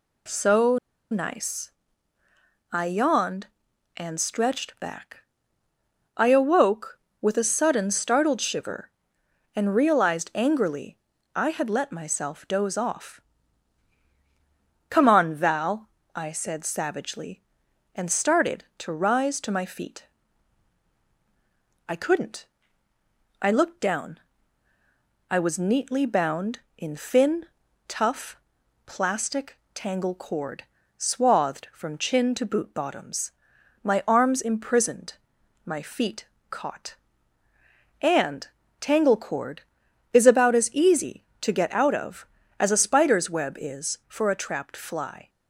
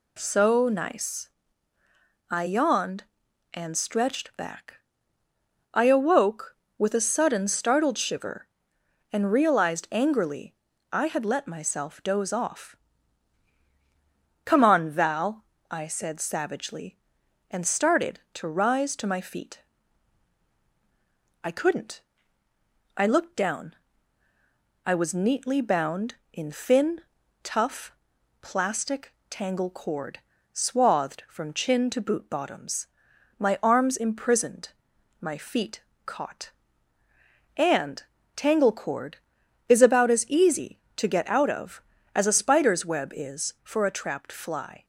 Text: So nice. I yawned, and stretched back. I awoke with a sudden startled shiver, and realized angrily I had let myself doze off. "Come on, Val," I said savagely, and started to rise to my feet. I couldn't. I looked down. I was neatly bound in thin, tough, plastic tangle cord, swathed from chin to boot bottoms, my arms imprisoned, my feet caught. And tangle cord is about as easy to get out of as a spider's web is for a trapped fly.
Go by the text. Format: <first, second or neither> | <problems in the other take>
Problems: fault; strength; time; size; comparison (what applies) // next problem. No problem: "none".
second | pauses between "So" and "nice"; slight; at 0.7 s; 0.34 s long // pauses between "angrily" and "I"; slight; at 10.9 s; 0.36 s long; slight in the second // pauses between "plastic" and "tangle"; slight; at 29.5 s; 0.18 s long; slight in the second // pauses between "feet" and "caught"; slight; at 36.2 s; 0.22 s long; slight in the second // pauses between "And" and "tangle"; slight; at 38.4 s; 0.32 s long; slight in the second